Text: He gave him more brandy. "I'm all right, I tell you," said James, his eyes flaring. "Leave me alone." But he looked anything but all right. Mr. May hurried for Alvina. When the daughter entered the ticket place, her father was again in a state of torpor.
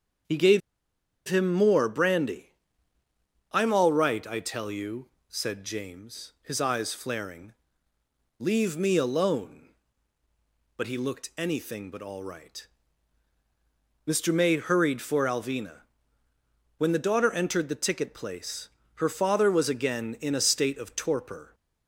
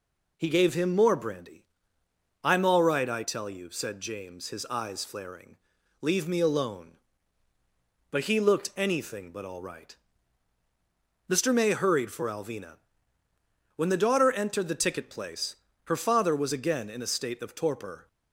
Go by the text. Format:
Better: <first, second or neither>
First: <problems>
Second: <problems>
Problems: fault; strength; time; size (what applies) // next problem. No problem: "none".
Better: second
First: starts louder than the rest; strong; until 1.9 s; 7.5 dB // pauses between "gave" and "him"; noticeable; at 0.6 s; 0.67 s long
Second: none